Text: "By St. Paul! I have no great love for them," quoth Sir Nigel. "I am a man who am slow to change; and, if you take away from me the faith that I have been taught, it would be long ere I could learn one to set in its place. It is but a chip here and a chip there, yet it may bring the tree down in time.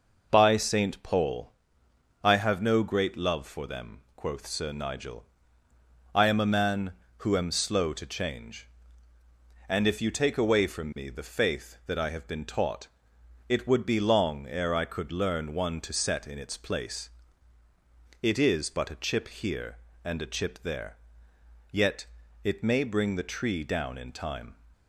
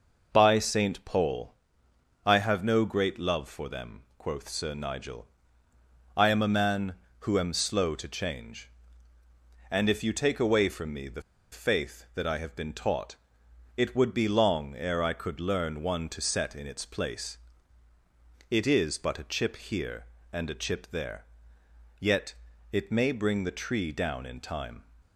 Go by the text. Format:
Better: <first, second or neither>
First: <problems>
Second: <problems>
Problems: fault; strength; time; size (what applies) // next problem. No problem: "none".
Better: first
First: pauses between "yet" and "it"; slight; at 22.0 s; 0.36 s long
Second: pauses between "the" and "faith"; slight; at 11.2 s; 0.31 s long // pauses between "yet" and "it"; slight; at 22.3 s; 0.36 s long